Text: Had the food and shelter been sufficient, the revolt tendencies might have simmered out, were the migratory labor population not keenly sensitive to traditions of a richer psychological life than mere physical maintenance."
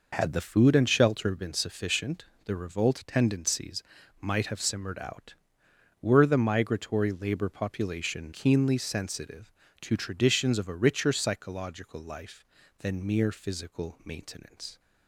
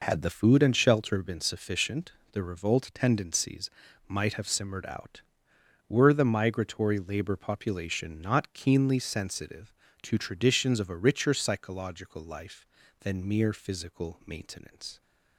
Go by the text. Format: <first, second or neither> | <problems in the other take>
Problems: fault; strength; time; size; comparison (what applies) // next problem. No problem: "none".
second | pauses between "tendencies" and "might"; at 3.8 s; 0.40 s long; also in the second // skips "not"; at 8.3 s